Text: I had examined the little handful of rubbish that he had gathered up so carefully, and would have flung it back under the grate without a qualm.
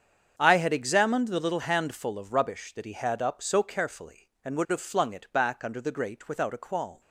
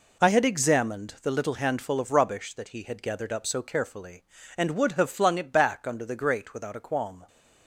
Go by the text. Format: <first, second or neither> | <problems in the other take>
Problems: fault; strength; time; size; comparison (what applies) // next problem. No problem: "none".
second | starts louder than the rest; strong; until 1.3 s; 7.5 dB // skips "gathered"; at 3.2 s